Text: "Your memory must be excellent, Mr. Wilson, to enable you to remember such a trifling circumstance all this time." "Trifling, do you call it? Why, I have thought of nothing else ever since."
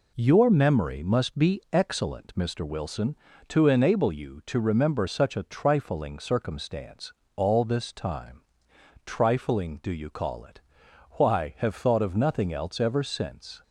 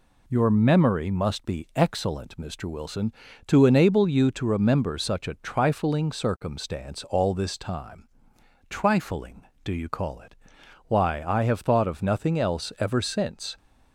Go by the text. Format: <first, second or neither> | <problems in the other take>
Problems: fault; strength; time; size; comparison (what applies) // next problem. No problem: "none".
second | pauses between "circumstance" and "all"; slight; at 7.1 s; 0.20 s long // skips "I"; at 11.5 s